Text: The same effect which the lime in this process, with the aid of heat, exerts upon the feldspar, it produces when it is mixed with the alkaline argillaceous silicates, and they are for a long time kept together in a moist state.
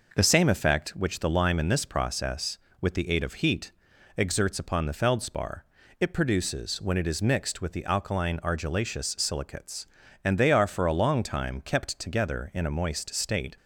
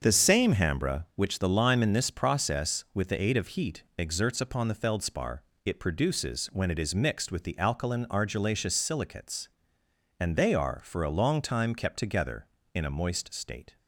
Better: first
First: none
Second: starts louder than the rest; until 1.0 s; 7 dB // says "hambra" for "effect"; at 0.5 s

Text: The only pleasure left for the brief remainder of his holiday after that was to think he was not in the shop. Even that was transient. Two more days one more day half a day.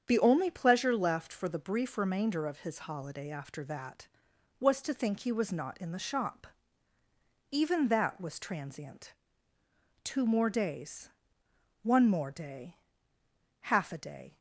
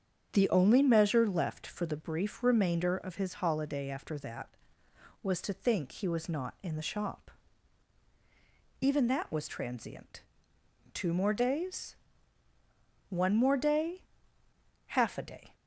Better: first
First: starts louder than the rest; strong; until 1.0 s; 7.5 dB // pauses between "days" and "one"; noticeable; at 11.0 s; 0.74 s long // pauses between "day" and "half"; noticeable; at 12.7 s; 0.82 s long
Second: starts louder than the rest; strong; until 1.3 s; 7.5 dB // says "measure" for "pleasure"; at 0.8 s // pauses between "days" and "one"; at 11.9 s; 1.1 s long // pauses between "day" and "half"; noticeable; at 14.0 s; 0.84 s long

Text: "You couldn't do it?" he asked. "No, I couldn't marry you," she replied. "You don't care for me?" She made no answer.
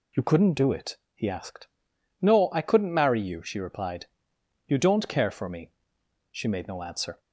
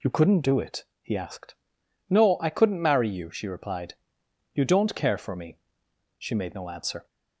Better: neither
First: none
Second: none

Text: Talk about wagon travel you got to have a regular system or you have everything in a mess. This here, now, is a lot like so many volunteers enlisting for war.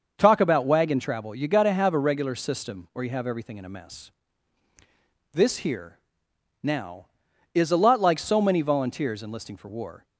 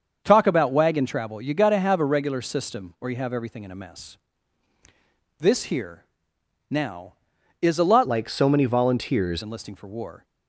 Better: first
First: starts louder than the rest; noticeable; until 1.1 s; 6 dB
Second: starts louder than the rest; until 1.2 s; 6.5 dB // changes voice from "like" to "volunteers"; from 8.0 to 9.4 s; 1.4 s long

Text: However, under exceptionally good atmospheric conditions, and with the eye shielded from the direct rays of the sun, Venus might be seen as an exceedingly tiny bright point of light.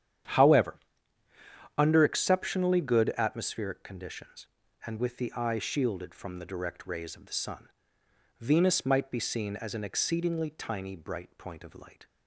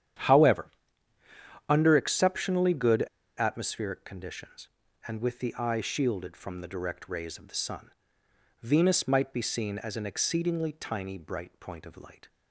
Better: first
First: starts louder than the rest; strong; until 2.2 s; 9.5 dB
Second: starts louder than the rest; strong; until 2.2 s; 9.5 dB // pauses between "good" and "atmospheric"; slight; at 3.0 s; 0.32 s long

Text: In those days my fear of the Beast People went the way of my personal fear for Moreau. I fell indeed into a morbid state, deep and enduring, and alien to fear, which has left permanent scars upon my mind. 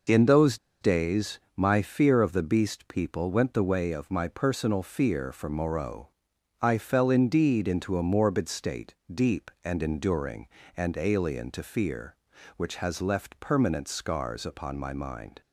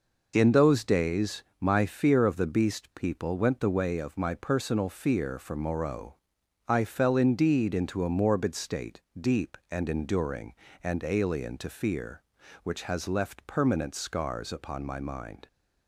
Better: second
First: pauses between "those" and "days"; slight; at 0.5 s; 0.24 s long // pauses between "days" and "my"; slight; at 1.4 s; 0.16 s long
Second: pauses between "days" and "my"; slight; at 1.4 s; 0.16 s long

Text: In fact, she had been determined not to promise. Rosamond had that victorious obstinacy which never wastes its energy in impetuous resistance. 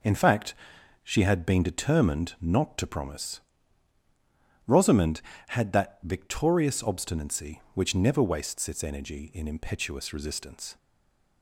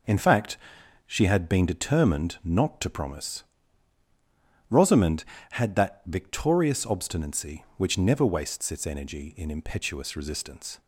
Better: second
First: stays silent after the last word; slight; from 10.7 s on; 0.7 s long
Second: none

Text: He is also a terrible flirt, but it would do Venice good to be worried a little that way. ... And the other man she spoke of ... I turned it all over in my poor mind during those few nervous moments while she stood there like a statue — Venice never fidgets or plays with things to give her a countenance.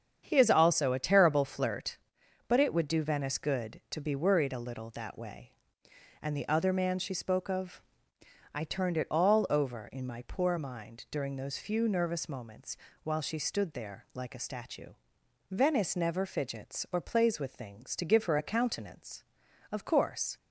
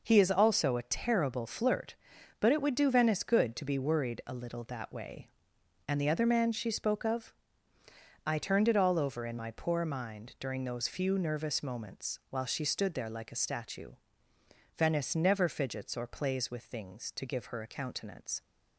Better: second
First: starts louder than the rest; strong; until 1.2 s; 7.5 dB // pauses between "moments" and "while"; slight; at 12.7 s; 0.26 s long // goes on to say "Of course"; noticeable; from 19.7 s on; 0.64 s long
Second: none

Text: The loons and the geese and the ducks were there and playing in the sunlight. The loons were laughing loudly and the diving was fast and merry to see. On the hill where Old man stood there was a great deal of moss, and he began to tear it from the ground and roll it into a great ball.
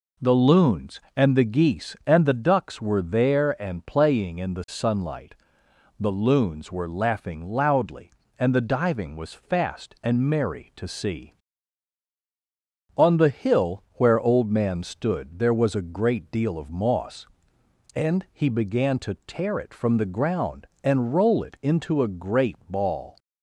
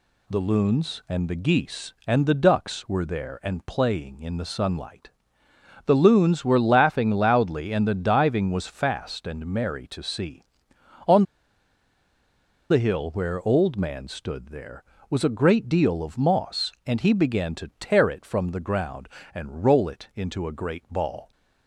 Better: first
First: none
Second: pauses between "On" and "the"; strong; at 11.2 s; 1.4 s long

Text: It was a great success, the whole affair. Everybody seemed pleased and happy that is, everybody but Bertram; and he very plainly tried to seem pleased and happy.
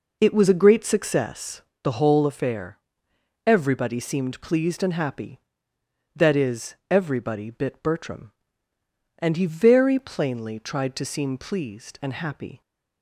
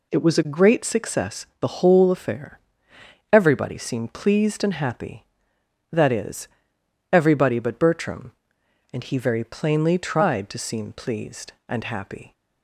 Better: second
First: says "bit" for "but"; at 7.4 s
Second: none

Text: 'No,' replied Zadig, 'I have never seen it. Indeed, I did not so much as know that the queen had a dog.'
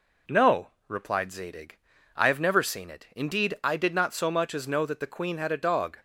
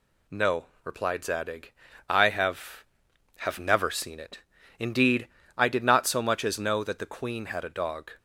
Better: first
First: none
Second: says "have" twice; at 3.3 s

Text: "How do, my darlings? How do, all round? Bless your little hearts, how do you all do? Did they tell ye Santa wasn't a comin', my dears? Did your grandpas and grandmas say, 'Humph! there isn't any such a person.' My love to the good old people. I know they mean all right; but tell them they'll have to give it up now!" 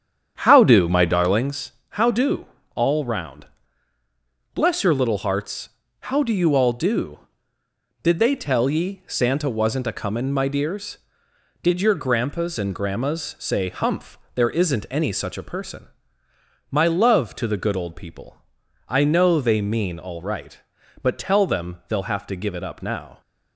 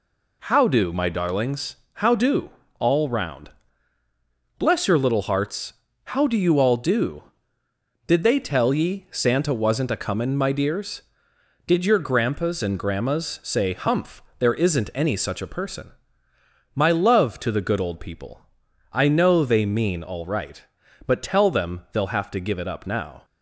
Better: second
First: starts louder than the rest; strong; until 1.5 s; 8.5 dB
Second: none

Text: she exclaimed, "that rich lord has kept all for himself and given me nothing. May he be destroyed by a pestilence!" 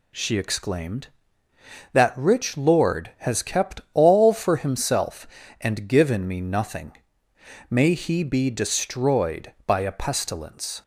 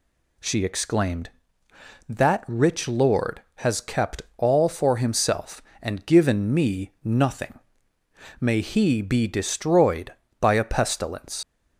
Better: first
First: none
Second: pauses between "kept" and "all"; slight; at 4.2 s; 0.16 s long // leaves "pestilence" unfinished; at 11.4 s; 65 ms

